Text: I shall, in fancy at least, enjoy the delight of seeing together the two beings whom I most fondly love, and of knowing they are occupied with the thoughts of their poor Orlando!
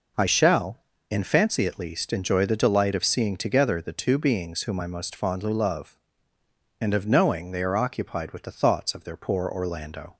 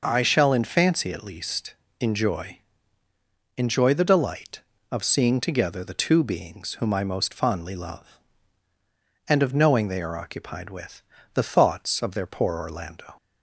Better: first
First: none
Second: says "enjoy" twice; at 3.5 s // pauses between "with" and "the"; slight; at 11.0 s; 0.32 s long

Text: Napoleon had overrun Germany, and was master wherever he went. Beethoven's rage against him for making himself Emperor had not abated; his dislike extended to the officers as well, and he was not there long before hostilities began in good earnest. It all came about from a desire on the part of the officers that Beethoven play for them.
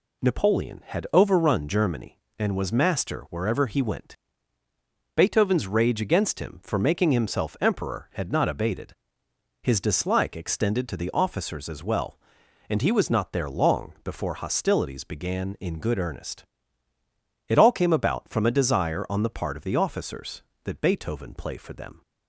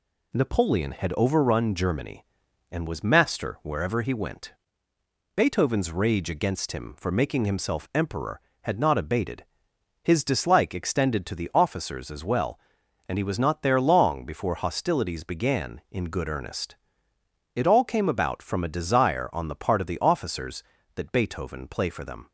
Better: neither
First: none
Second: none

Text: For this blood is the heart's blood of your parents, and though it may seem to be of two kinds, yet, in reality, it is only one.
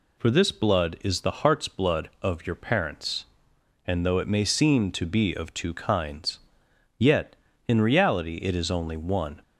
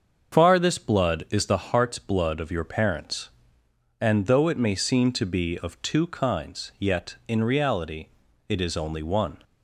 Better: first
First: none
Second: starts louder than the rest; until 1.3 s; 7 dB // says "Far" for "For"; at 0.3 s

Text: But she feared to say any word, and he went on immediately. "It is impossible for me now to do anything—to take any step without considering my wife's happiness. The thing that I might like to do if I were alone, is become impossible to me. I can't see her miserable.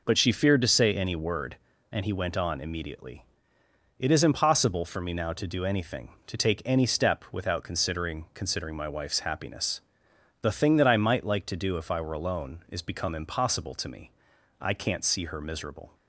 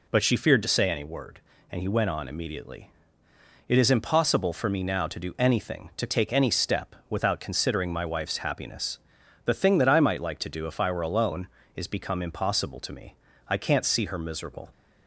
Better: second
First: says "considering" twice; at 8.3 s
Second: none

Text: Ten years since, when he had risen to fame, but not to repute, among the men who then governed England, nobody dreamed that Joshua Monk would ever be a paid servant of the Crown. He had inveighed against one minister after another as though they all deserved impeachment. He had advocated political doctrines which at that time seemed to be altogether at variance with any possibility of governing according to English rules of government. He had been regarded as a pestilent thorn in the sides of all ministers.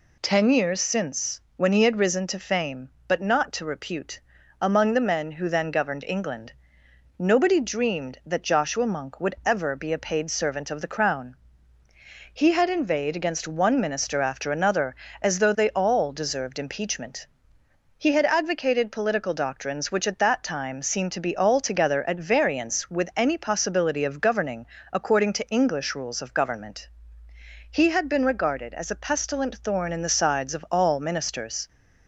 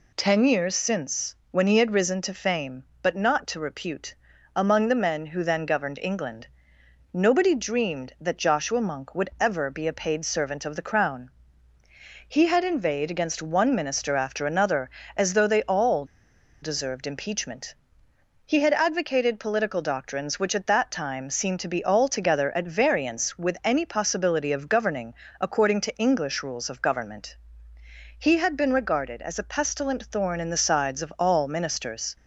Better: first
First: pauses between "governing" and "according"; slight; at 24.6 s; 0.24 s long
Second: pauses between "all" and "deserved"; noticeable; at 16.0 s; 0.57 s long // pauses between "governing" and "according"; slight; at 25.1 s; 0.24 s long

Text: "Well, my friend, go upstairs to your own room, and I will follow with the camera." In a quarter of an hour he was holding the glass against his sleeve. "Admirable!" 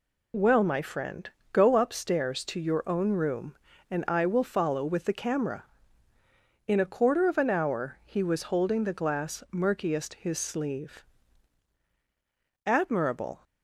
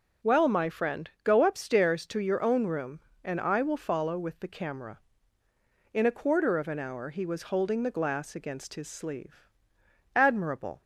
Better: second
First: says "murkiest" for "against"; at 9.5 s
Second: none

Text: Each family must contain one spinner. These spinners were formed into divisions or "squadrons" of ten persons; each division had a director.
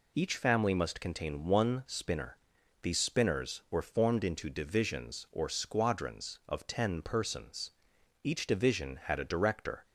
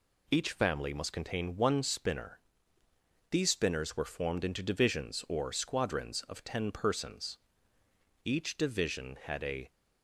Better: first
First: none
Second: stops before "director"; at 9.6 s

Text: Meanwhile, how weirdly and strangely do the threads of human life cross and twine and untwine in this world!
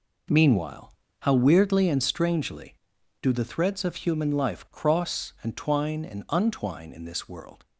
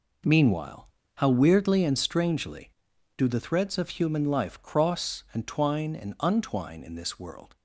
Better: neither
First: none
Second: none

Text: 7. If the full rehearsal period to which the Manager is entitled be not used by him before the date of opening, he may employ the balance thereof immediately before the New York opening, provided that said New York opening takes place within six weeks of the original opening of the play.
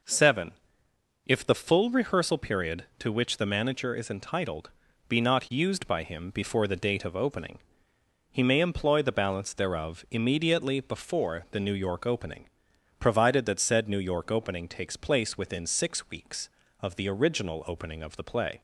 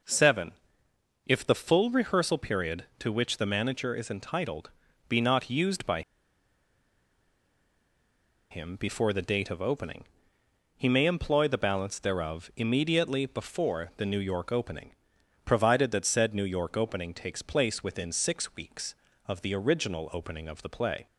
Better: first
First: pauses between "entitled" and "be"; at 4.6 s; 0.38 s long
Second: pauses between "entitled" and "be"; at 4.6 s; 0.38 s long // pauses between "by" and "him"; strong; at 6.0 s; 2.5 s long

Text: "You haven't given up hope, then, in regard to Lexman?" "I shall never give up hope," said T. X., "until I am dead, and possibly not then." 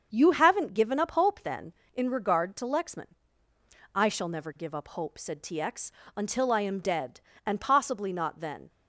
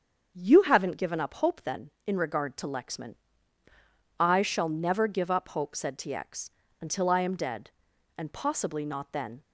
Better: neither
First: starts louder than the rest; until 1.1 s; 7 dB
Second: starts louder than the rest; until 1.3 s; 7 dB

